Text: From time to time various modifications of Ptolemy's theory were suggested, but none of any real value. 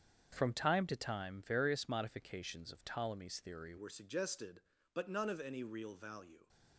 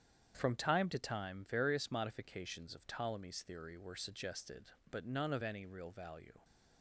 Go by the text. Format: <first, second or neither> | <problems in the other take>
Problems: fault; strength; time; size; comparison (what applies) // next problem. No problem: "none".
second | starts louder than the rest; strong; until 1.3 s; 8 dB; strong in the second // changes voice at "were"; from 3.7 s on; 2.7 s long